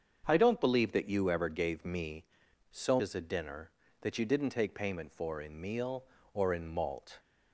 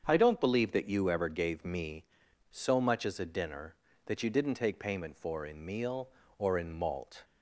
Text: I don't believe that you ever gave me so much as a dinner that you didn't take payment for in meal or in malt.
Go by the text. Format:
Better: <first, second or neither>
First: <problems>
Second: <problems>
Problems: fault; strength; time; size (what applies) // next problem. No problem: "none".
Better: second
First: starts louder than the rest; until 1.2 s; 7 dB // skips "much"; at 3.0 s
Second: starts louder than the rest; strong; until 1.0 s; 7.5 dB